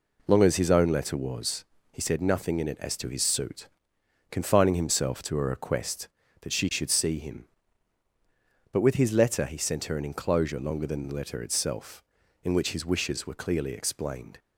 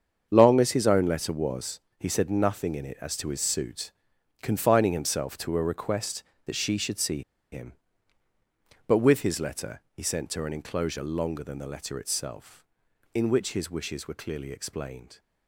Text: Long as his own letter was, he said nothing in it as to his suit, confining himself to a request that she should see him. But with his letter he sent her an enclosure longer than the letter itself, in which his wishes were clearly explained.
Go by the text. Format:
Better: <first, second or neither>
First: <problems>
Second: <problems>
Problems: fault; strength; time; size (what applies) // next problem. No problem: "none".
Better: first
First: none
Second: starts louder than the rest; strong; until 1.3 s; 7.5 dB // pauses between "see" and "him"; slight; at 7.2 s; 0.29 s long